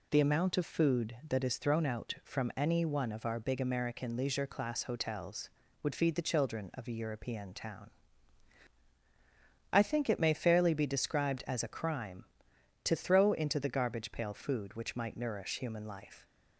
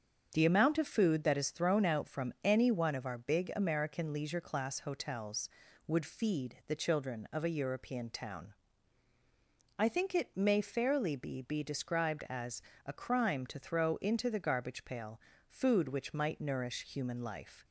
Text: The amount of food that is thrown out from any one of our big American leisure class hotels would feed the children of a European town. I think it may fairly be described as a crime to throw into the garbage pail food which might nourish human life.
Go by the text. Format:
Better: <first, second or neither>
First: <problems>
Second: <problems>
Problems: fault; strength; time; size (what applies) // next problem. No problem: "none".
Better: first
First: none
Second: starts louder than the rest; strong; until 1.3 s; 7.5 dB // says "be" twice; at 11.3 s // pauses between "as" and "a"; slight; at 12.5 s; 0.24 s long // pauses between "pail" and "food"; slight; at 15.1 s; 0.28 s long